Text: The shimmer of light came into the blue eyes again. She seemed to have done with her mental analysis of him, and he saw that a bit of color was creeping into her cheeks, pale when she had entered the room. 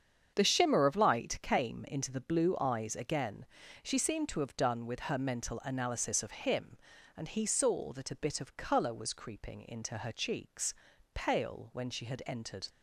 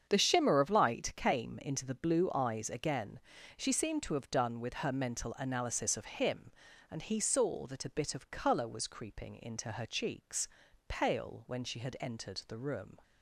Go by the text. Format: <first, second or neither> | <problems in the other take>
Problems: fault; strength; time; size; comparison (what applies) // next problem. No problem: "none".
second | starts louder than the rest; strong; until 1.3 s; 7.5 dB; strong in the second // stops before "the room"; at 12.6 s